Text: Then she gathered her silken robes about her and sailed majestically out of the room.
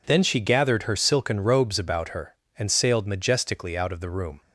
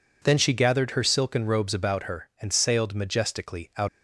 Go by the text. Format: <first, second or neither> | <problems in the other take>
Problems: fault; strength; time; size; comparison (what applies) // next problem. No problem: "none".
first | stops before "of the room"; at 3.8 s